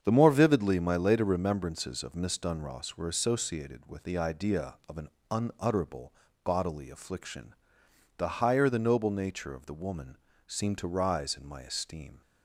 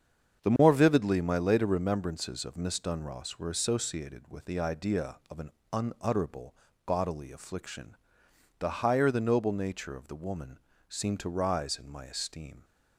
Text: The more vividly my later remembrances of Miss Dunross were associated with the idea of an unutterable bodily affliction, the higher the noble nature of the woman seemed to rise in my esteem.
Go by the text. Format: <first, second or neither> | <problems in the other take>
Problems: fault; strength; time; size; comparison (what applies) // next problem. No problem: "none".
neither | starts louder than the rest; strong; the same in both // pauses between "an" and "unutterable"; slight; the same in both // pauses between "unutterable" and "bodily"; slight; the same in both // pauses between "woman" and "seemed"; slight; the same in both